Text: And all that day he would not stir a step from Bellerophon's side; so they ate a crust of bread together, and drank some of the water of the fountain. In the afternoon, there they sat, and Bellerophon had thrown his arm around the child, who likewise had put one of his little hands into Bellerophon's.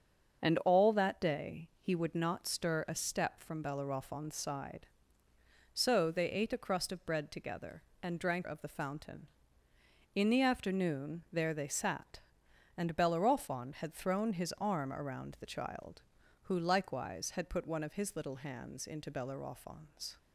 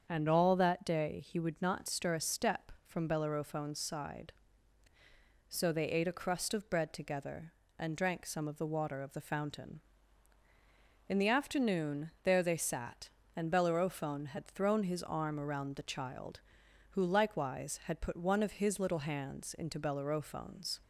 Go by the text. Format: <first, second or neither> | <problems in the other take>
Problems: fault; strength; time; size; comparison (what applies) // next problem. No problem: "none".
second | starts louder than the rest; until 1.4 s; 6.5 dB; strong in the second // skips "some of the water"; at 8.4 s